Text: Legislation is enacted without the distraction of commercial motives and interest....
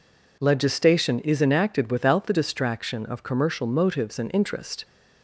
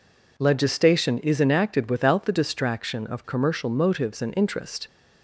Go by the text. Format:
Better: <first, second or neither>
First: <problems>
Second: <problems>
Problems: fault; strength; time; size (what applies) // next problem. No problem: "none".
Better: neither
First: none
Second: none